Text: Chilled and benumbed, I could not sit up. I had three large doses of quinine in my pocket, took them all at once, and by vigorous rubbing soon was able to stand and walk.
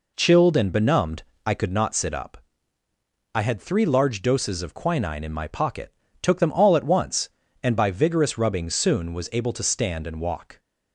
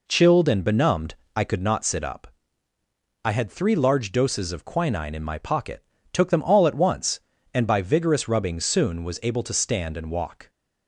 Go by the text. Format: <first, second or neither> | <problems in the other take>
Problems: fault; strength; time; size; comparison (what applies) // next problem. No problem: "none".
neither | none